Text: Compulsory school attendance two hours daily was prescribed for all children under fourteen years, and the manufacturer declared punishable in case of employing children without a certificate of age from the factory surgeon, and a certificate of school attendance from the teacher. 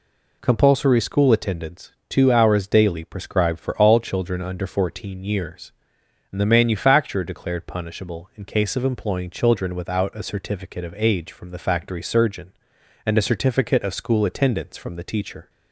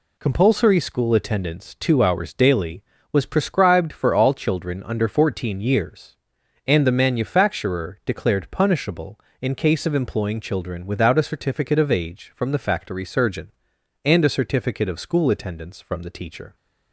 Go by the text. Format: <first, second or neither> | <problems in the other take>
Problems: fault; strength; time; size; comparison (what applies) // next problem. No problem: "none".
second | pauses between "attendance" and "two"; slight; at 1.9 s; 0.16 s long // skips "was"; at 3.0 s